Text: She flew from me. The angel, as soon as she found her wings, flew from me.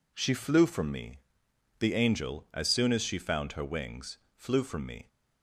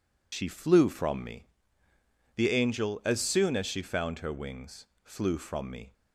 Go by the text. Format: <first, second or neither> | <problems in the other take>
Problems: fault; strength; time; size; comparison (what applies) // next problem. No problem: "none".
first | loses the start of "She"; at 0.3 s; 60 ms